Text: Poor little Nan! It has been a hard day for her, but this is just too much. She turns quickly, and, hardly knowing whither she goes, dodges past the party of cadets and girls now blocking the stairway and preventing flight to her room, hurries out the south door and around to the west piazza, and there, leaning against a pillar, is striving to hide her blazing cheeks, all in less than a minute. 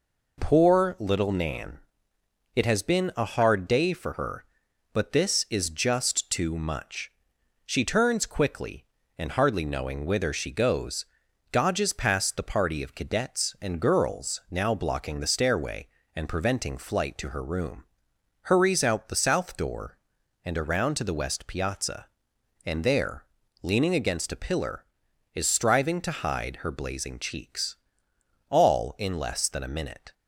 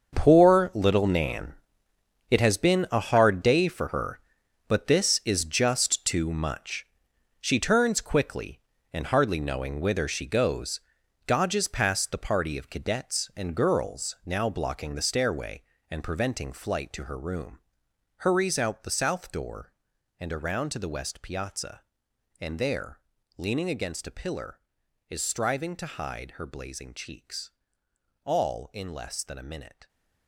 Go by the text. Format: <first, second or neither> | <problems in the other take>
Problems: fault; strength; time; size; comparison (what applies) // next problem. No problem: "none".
first | gets quieter; strong; throughout; 13.5 dB